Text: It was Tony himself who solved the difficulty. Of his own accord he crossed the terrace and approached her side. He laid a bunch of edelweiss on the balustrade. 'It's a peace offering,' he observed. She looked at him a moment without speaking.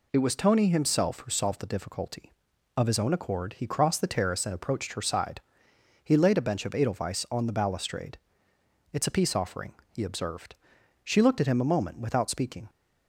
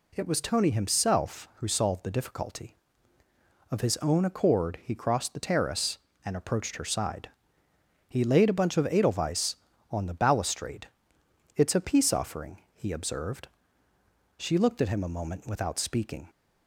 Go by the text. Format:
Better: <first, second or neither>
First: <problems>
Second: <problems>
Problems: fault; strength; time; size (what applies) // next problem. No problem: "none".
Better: second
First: says "bench" for "bunch"; at 6.4 s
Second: none